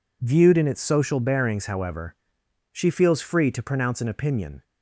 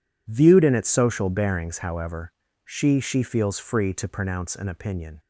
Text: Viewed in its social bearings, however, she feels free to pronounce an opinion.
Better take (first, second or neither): first